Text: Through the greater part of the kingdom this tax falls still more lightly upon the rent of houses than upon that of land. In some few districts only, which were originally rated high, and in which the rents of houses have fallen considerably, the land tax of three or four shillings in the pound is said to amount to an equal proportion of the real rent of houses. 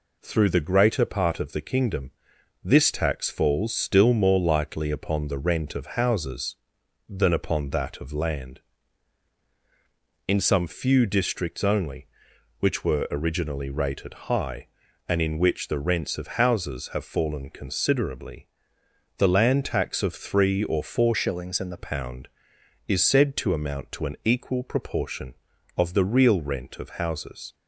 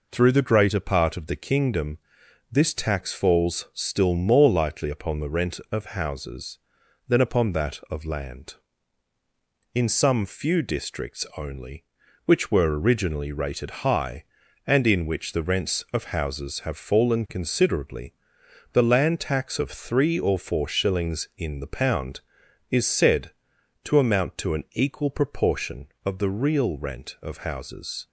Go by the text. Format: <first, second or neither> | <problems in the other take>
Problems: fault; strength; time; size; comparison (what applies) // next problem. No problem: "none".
second | pauses between "kingdom" and "this"; noticeable; at 2.1 s; 0.52 s long; noticeable in the second // changes voice from "shillings" to "the"; from 21.1 to 21.7 s; 0.6 s long